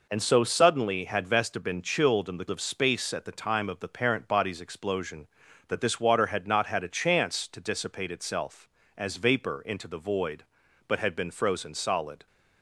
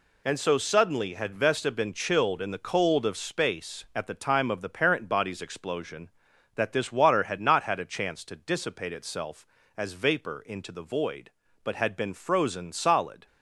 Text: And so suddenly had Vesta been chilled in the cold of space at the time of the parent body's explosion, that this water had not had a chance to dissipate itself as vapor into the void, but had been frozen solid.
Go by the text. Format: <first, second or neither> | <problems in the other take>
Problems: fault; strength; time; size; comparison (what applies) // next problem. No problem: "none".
second | skips "cold"; at 2.4 s